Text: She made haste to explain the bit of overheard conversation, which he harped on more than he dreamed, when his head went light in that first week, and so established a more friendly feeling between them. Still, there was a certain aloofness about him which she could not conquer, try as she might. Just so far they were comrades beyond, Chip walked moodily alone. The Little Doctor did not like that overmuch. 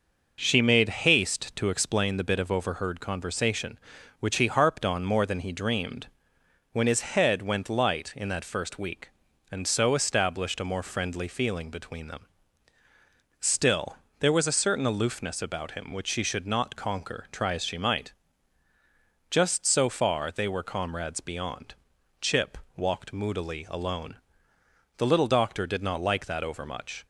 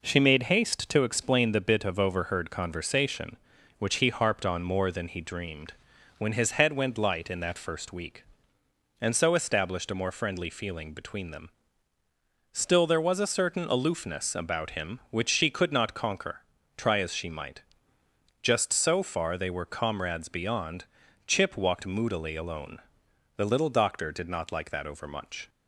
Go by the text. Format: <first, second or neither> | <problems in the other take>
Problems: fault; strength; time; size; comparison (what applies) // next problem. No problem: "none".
second | says "should" for "could"; at 16.2 s // pauses between "Chip" and "walked"; slight; at 22.5 s; 0.20 s long